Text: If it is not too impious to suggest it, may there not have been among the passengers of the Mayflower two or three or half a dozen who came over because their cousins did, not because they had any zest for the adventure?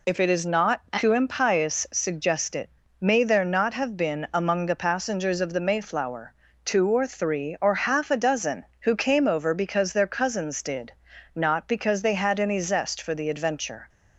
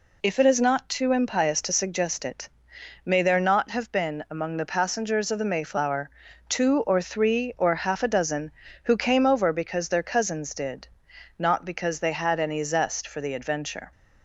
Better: second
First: skips "to"; at 1.8 s // pauses between "Mayflower" and "two"; slight; at 6.3 s; 0.30 s long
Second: pauses between "Mayflower" and "two"; at 6.1 s; 0.38 s long

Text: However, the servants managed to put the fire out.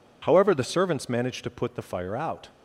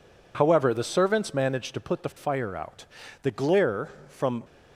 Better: first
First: none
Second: goes on to say "The glare from"; noticeable; from 3.2 s on; 1.2 s long

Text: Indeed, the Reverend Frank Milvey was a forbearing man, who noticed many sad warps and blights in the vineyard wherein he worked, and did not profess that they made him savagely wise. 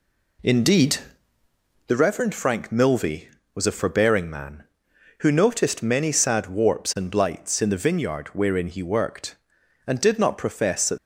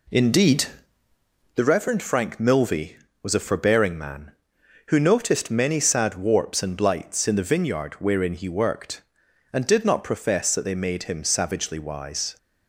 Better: second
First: stops before "they made him savagely wise"; at 10.9 s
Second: none

